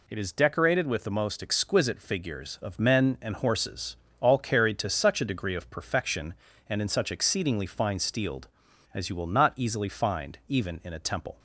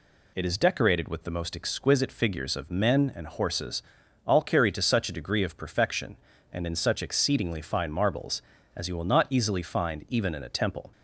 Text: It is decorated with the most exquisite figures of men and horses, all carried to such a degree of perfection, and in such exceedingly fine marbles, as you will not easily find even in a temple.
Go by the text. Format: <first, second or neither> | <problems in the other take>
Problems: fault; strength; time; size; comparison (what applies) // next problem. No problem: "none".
second | says "steeled" for "marbles"; at 7.9 s